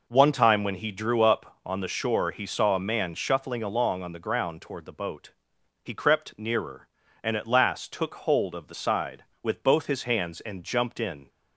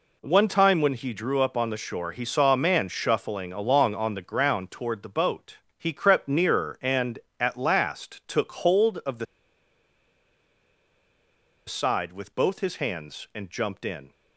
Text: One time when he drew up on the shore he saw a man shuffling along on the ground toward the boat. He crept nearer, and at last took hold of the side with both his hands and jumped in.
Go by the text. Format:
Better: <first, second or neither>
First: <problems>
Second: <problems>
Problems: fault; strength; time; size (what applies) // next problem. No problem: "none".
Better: first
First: none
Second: pauses between "the" and "side"; strong; at 9.2 s; 2.4 s long